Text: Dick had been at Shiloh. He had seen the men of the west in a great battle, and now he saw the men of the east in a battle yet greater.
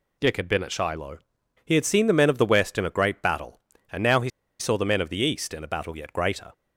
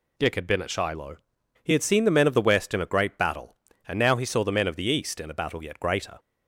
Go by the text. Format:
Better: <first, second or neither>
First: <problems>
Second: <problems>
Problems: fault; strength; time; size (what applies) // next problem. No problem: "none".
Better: second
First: pauses between "he" and "saw"; slight; at 4.2 s; 0.29 s long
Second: none